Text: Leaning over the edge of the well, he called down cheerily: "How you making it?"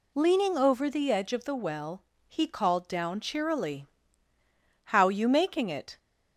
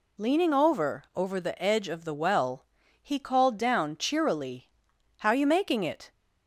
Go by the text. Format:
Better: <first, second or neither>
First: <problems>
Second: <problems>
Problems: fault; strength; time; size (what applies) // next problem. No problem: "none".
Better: first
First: none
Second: says "over" twice; at 1.1 s